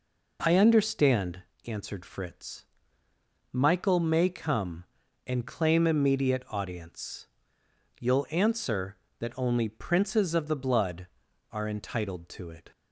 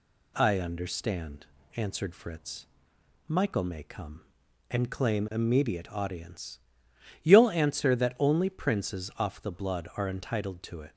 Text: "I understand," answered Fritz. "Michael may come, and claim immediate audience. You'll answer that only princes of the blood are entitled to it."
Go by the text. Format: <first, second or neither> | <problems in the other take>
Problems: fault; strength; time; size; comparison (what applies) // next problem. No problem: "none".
first | says "off" for "of"; at 9.1 s